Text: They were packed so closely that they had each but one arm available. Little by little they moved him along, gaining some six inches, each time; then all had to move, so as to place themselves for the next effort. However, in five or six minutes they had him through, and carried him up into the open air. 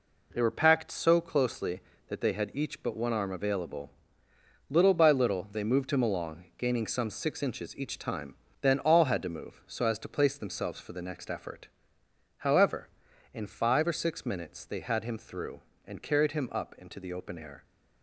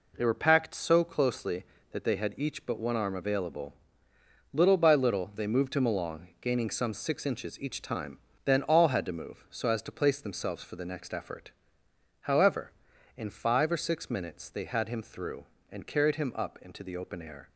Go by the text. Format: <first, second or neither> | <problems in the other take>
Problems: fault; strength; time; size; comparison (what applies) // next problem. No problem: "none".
neither | none